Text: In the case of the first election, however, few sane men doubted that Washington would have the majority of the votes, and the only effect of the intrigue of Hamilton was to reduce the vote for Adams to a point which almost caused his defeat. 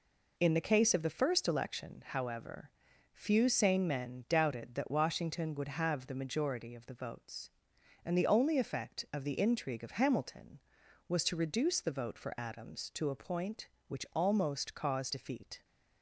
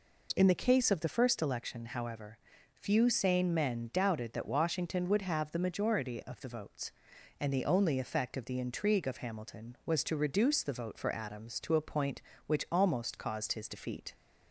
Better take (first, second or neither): second